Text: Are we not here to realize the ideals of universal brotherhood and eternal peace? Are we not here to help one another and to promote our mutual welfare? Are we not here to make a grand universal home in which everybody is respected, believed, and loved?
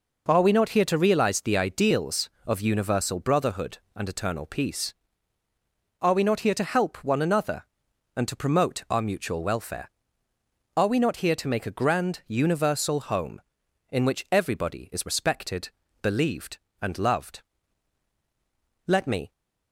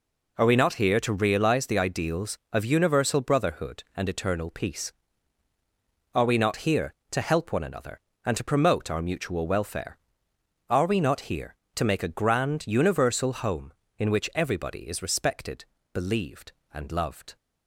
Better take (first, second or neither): second